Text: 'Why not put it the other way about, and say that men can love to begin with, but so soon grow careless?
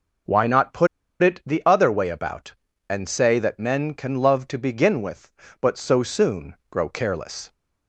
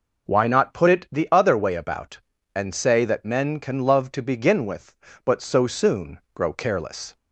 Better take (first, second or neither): second